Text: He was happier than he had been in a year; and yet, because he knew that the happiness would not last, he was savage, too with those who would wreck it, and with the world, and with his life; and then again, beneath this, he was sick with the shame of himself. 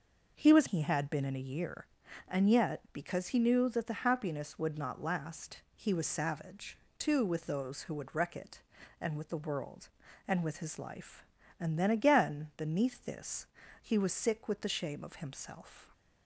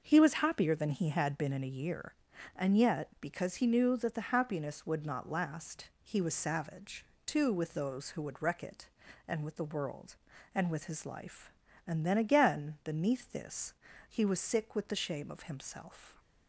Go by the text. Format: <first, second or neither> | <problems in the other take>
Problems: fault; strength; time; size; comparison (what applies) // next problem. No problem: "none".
second | starts louder than the rest; until 1.3 s; 6 dB; also in the second // skips "happier than"; at 0.6 s